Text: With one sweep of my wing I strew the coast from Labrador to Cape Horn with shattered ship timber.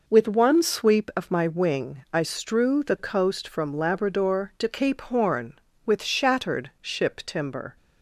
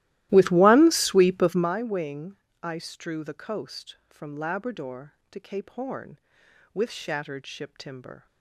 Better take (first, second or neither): first